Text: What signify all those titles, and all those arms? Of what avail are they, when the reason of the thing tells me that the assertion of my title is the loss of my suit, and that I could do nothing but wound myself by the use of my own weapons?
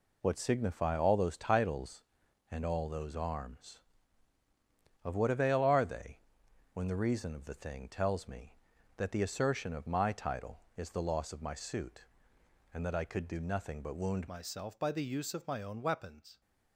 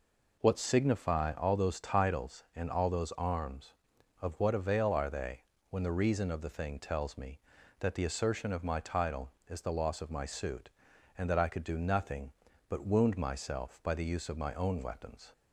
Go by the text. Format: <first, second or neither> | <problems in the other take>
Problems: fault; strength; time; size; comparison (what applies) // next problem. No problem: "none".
second | changes voice at "myself"; from 14.2 s on; 2.2 s long